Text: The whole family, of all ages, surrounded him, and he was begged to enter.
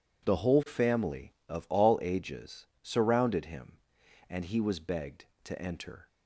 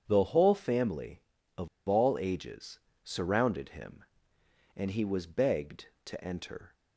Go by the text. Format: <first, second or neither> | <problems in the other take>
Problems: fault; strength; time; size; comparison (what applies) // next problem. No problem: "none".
first | starts louder than the rest; strong; until 1.0 s; 8 dB // pauses between "of" and "all"; slight; at 1.6 s; 0.19 s long